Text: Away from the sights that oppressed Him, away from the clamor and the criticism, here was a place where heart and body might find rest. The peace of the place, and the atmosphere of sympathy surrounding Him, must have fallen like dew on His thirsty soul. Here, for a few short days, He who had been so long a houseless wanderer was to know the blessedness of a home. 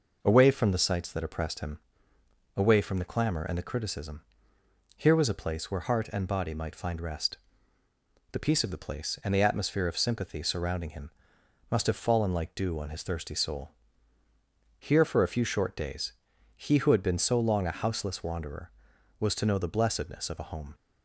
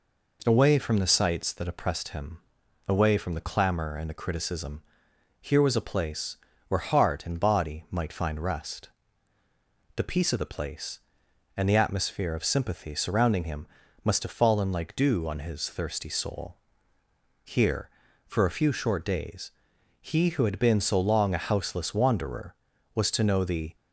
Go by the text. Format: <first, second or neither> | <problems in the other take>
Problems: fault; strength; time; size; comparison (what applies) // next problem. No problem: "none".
first | pauses between "place" and "where"; slight; at 6.3 s; 0.30 s long // stops before "blessedness of a home"; at 23.7 s